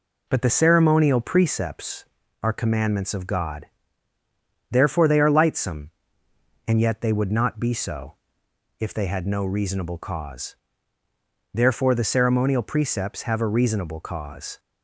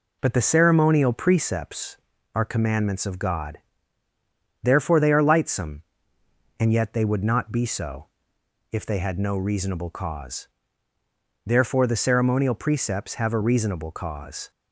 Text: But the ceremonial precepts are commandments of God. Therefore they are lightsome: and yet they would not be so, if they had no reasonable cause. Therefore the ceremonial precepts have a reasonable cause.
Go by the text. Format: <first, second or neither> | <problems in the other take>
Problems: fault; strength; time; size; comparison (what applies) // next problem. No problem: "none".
neither | none